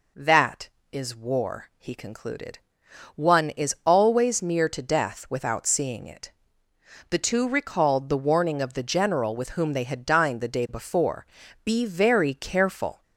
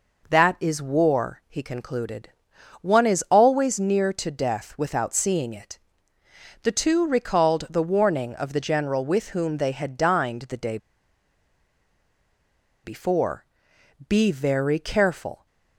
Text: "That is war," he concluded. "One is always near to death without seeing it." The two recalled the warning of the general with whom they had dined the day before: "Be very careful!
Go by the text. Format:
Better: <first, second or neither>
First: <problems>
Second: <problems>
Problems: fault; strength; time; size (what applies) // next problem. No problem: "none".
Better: first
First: none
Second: pauses between "day" and "before"; strong; at 10.7 s; 2.0 s long